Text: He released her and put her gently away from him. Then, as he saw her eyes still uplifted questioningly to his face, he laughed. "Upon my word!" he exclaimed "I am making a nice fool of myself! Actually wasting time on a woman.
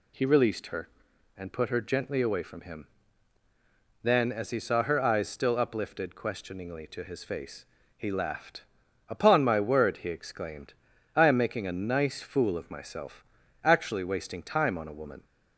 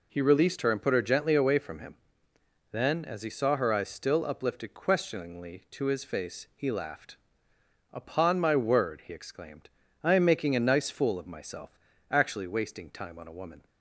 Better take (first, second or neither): neither